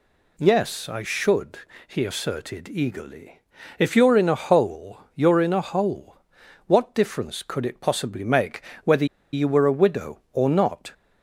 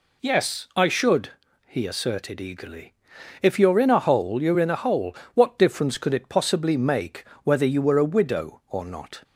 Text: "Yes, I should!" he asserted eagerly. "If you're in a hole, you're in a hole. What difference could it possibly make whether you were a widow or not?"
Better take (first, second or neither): second